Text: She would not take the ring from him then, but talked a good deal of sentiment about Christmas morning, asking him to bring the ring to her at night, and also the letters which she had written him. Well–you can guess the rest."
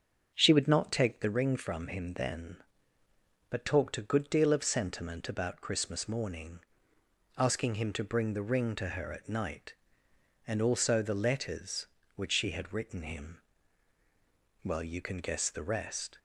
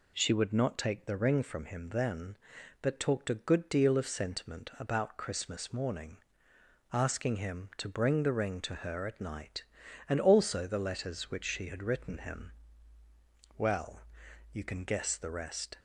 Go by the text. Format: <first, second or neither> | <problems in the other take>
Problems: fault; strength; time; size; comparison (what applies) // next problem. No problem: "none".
second | starts louder than the rest; strong; until 1.4 s; 7 dB